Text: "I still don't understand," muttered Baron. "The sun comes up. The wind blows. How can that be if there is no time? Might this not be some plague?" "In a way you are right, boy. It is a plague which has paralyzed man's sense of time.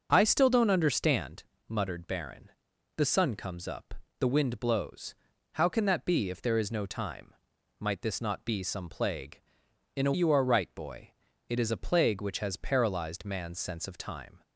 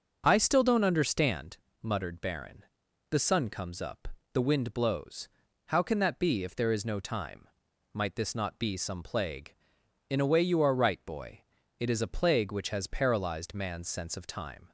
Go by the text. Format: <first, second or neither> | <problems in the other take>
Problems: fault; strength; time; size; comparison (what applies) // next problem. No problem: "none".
second | starts louder than the rest; until 1.1 s; 6.5 dB; also in the second // skips "way"; at 10.1 s